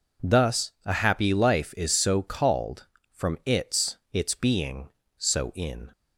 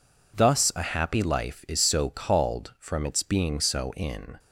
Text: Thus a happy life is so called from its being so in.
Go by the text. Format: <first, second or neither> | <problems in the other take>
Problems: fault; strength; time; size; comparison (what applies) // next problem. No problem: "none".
second | says "its" twice; at 4.1 s